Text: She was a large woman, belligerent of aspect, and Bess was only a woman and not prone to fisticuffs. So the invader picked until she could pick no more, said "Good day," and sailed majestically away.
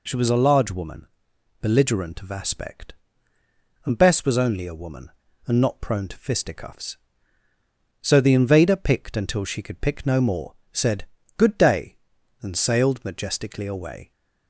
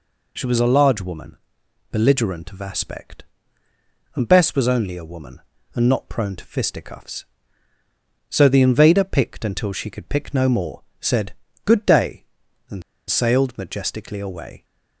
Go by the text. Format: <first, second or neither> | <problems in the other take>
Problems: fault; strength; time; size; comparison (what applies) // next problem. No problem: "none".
first | pauses between "said" and "Good"; slight; at 11.3 s; 0.32 s long; slight in the first // pauses between "and" and "sailed"; slight; at 12.8 s; 0.27 s long